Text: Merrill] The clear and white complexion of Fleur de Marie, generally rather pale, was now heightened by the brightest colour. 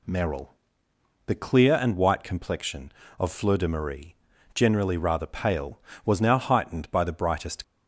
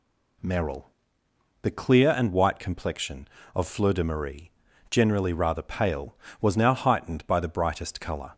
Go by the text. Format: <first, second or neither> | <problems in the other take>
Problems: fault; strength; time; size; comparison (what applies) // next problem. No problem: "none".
second | pauses between "Merrill" and "The"; noticeable; at 0.5 s; 0.72 s long; noticeable in the second // stops before "colour"; at 7.6 s